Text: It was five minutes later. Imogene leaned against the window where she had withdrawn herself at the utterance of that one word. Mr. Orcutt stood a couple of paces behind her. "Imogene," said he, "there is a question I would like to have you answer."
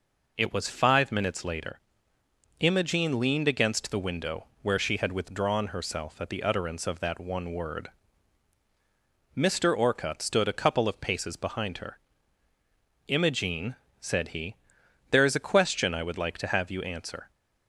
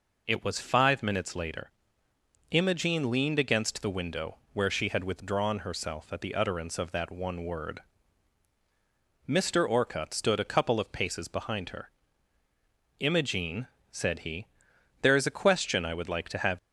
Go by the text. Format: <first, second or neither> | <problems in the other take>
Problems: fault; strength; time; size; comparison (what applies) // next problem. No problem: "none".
first | pauses between "window" and "where"; slight; at 4.3 s; 0.18 s long; slight in the first // stops before "you answer"; at 16.5 s